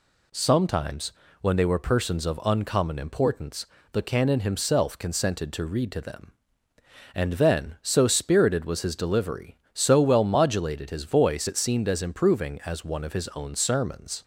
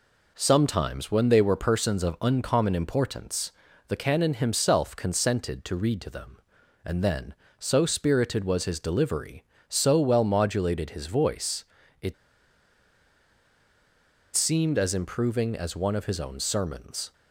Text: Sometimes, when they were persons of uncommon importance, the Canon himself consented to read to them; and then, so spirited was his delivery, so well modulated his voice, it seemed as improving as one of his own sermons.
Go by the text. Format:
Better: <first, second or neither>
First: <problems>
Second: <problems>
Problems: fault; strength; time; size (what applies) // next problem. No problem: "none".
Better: first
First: none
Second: pauses between "it" and "seemed"; strong; at 12.1 s; 2.2 s long